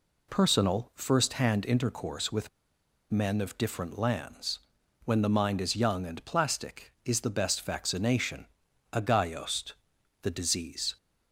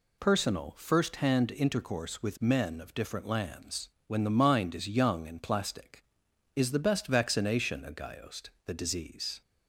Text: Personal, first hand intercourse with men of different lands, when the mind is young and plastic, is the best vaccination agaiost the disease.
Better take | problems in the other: second | pauses between "with" and "men"; noticeable; at 2.4 s; 0.63 s long // pauses between "vaccination" and "agaiost"; noticeable; at 8.4 s; 0.48 s long // pauses between "agaiost" and "the"; noticeable; at 9.7 s; 0.50 s long; slight in the second

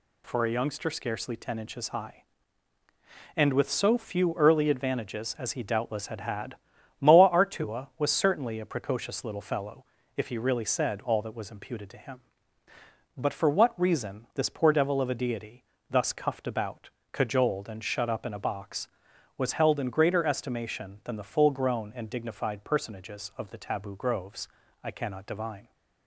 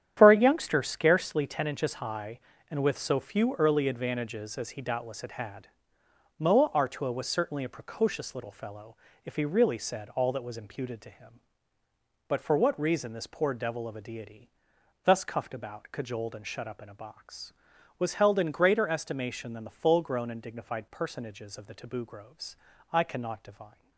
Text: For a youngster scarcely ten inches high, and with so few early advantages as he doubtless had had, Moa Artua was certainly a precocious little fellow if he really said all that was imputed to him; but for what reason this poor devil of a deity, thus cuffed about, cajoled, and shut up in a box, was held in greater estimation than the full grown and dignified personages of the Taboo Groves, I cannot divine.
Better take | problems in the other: first | gets quieter; strong; throughout; 11.5 dB // pauses between "fellow" and "if"; slight; at 8.9 s; 0.28 s long; slight in the first

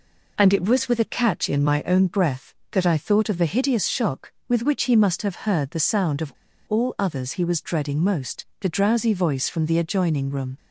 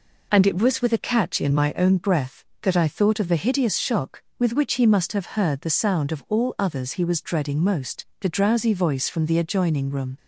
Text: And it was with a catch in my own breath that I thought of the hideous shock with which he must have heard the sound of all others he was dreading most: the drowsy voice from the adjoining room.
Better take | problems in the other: second | pauses between "of" and "all"; slight; at 6.3 s; 0.34 s long

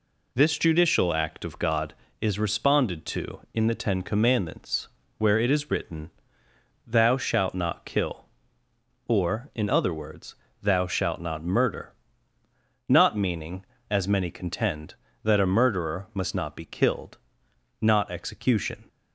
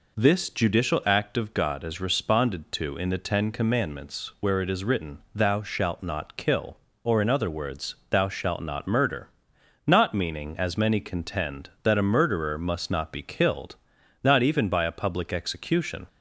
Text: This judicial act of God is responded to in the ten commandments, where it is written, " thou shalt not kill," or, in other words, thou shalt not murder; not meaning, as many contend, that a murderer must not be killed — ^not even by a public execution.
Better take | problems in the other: second | skips "even by a public"; at 18.0 s

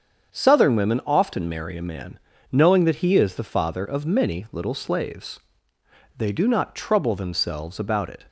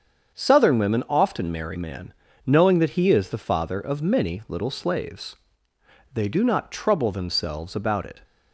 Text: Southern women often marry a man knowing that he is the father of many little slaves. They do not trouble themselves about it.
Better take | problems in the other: first | starts louder than the rest; strong; until 1.4 s; 7 dB; strong in the first // skips "a"; at 1.7 s // pauses between "man" and "knowing"; slight; at 2.1 s; 0.32 s long; slight in the first

